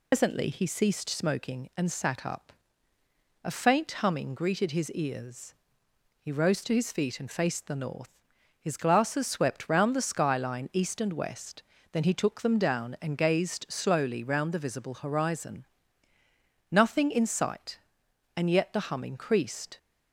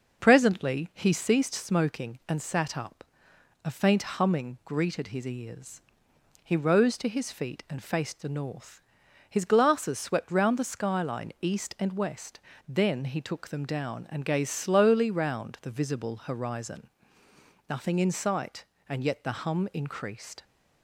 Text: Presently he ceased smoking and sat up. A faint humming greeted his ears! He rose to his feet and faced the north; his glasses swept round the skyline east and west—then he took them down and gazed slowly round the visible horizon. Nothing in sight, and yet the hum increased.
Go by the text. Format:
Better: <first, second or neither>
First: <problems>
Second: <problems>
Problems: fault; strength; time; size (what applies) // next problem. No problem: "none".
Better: second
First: loses the start of "Presently"; at 0.1 s; 145 ms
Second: none